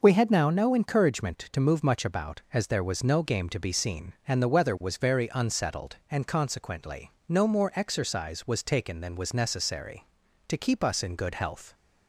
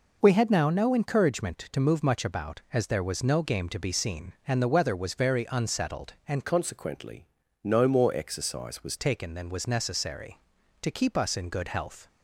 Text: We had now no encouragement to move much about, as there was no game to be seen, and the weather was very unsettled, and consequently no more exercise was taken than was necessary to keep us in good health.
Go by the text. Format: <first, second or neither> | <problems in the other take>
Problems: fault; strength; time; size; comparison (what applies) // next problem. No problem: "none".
first | changes voice from "consequently" to "was"; from 6.4 to 8.9 s; 2.5 s long // pauses between "consequently" and "no"; at 7.2 s; 0.40 s long; slight in the first